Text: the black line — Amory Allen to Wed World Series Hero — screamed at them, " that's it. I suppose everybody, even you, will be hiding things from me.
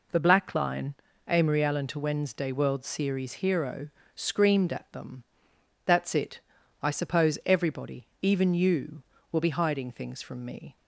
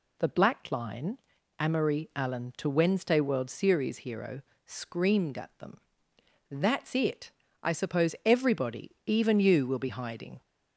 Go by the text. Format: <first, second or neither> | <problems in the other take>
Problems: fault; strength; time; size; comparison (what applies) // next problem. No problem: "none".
first | stops before "things from me"; at 10.4 s